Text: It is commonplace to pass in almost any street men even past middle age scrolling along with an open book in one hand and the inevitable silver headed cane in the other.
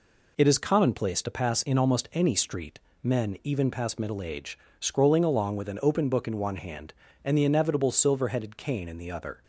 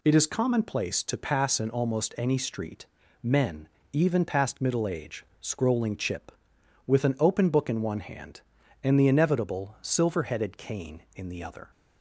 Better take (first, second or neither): first